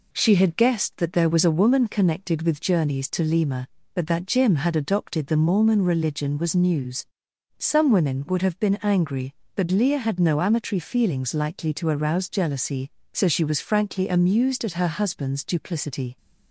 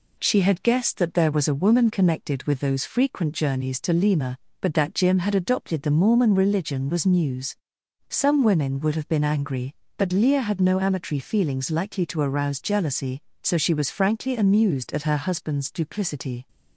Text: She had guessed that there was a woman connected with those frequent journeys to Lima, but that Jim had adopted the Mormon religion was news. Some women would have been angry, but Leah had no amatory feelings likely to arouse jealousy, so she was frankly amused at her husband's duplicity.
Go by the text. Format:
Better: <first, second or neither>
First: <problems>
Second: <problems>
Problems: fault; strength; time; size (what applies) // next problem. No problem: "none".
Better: second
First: skips "those frequent"; at 2.6 s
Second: none